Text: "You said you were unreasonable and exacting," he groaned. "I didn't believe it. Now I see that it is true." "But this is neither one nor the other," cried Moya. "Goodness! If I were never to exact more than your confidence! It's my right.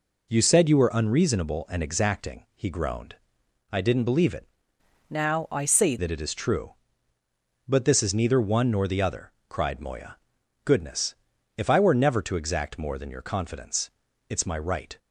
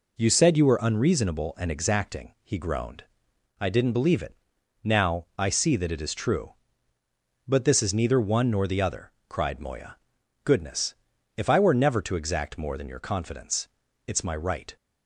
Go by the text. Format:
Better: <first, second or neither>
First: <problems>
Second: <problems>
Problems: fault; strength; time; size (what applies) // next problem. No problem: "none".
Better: second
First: changes voice from "Now" to "see"; from 5.0 to 5.9 s; 0.9 s long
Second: none